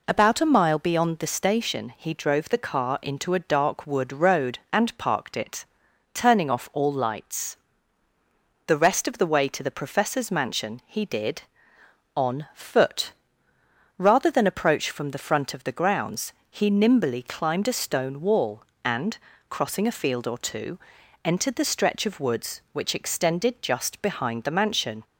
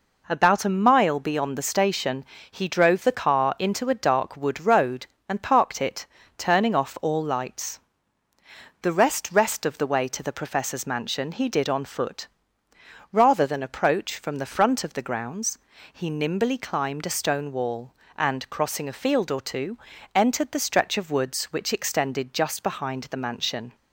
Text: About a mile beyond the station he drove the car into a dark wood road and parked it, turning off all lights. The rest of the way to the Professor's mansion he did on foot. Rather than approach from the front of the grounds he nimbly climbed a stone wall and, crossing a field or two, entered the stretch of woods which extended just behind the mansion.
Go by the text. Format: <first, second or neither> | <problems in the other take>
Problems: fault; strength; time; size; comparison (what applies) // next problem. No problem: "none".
first | pauses between "station" and "he"; slight; at 2.2 s; 0.26 s long // says "rest" twice; at 9.3 s // pauses between "grounds" and "he"; slight; at 15.5 s; 0.34 s long; slight in the first